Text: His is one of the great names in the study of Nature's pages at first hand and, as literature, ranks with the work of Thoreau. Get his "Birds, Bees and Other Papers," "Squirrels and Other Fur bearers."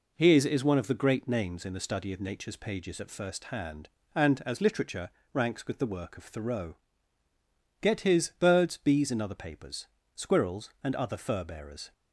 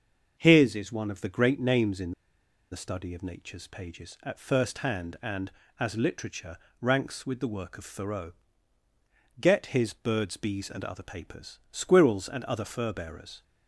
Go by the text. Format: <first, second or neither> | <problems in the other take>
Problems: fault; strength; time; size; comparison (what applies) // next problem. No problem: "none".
first | starts louder than the rest; until 1.3 s; 6.5 dB // pauses between "in" and "the"; noticeable; at 2.1 s; 0.60 s long